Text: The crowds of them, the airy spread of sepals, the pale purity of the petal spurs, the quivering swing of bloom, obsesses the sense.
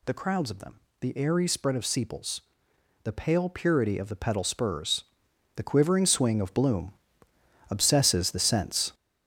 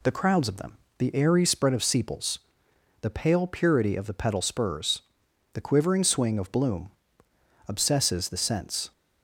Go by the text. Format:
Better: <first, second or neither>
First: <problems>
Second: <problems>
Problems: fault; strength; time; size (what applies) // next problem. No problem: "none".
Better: second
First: gets louder; strong; throughout; 8 dB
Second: none